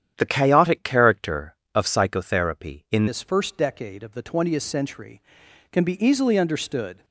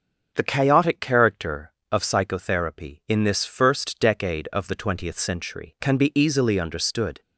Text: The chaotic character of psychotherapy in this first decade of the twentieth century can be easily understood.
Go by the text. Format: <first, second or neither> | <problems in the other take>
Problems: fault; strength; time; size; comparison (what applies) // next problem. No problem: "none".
second | starts louder than the rest; strong; until 1.1 s; 9.5 dB; noticeable in the second // changes voice at "this"; from 3.0 s on; 4.0 s long